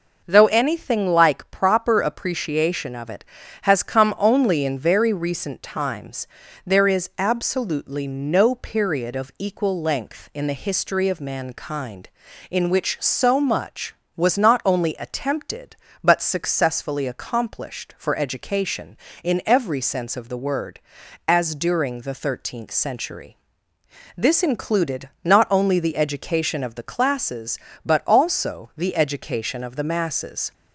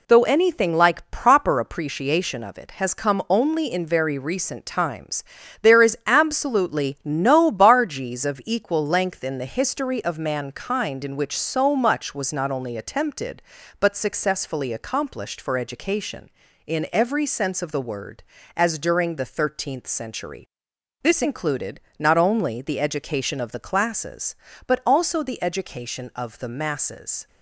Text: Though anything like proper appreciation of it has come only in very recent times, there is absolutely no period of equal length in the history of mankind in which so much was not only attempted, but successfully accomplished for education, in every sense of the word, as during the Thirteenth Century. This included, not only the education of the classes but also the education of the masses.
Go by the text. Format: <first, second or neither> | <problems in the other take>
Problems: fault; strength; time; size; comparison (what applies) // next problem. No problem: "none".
first | says "bargees" for "period"; at 7.5 s